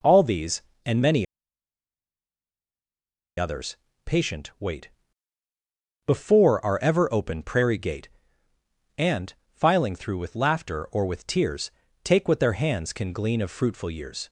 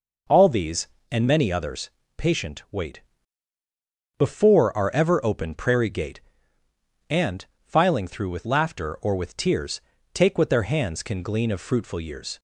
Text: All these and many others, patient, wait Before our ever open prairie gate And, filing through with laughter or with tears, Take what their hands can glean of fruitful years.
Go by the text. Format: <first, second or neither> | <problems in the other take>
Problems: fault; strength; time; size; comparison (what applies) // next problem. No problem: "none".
second | pauses between "many" and "others"; strong; at 1.2 s; 2.1 s long // pauses between "wait" and "Before"; at 4.8 s; 1.1 s long; also in the second